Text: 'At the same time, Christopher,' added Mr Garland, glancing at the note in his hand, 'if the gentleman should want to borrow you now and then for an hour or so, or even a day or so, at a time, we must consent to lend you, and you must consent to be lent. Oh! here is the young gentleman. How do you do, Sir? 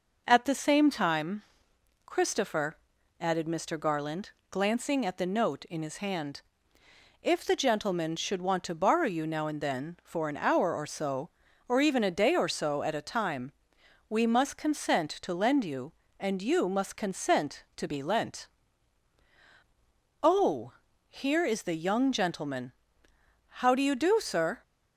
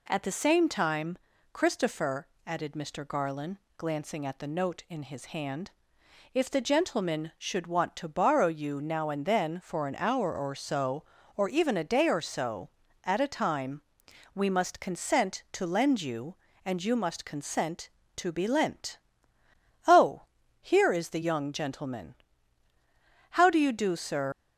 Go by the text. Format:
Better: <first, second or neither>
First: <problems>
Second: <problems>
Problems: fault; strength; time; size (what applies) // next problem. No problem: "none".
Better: first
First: none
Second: leaves "Sir" unfinished; at 24.3 s; 110 ms